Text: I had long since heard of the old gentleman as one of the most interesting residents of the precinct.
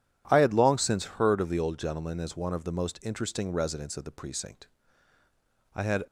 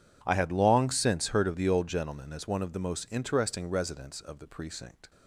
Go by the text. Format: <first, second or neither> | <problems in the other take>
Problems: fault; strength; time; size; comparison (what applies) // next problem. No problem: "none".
second | goes on to say "I had"; slight; from 5.7 s on; 0.30 s long